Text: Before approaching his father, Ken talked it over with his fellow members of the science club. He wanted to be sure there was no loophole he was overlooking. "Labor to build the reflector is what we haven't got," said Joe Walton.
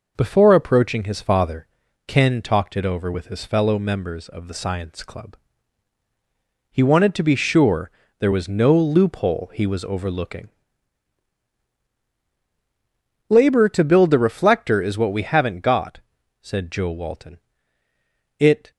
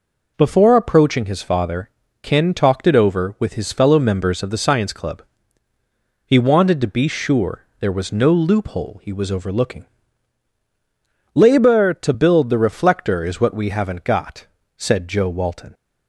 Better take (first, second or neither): second